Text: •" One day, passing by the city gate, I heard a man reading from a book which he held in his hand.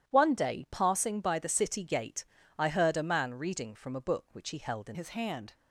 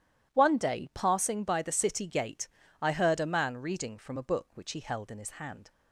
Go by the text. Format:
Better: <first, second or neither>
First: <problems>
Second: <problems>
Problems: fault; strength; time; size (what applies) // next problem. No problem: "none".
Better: second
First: starts louder than the rest; strong; until 1.1 s; 11 dB // changes voice at "his"; from 4.9 s on; 0.6 s long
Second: none